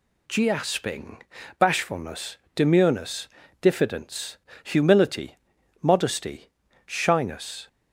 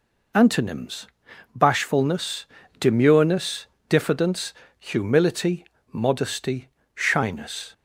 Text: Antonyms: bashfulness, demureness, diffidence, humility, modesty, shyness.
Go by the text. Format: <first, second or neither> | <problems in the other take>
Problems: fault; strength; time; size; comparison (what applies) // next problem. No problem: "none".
second | says "Giasping" for "Antonyms"; at 0.2 s